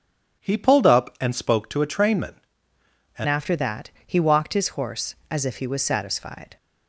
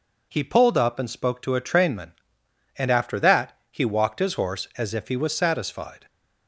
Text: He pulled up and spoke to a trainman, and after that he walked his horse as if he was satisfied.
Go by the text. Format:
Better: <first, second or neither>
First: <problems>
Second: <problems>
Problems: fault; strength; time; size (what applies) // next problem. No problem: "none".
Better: second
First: changes voice at "after"; from 3.2 s on; 3.3 s long // pauses between "that" and "he"; slight; at 3.8 s; 0.18 s long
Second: none